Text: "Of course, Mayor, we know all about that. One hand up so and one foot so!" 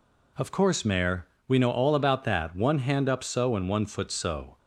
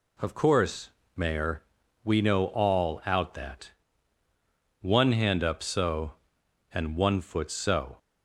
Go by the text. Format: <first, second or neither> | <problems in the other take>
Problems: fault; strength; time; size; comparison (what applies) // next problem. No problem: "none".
first | says "out" for "about"; at 3.0 s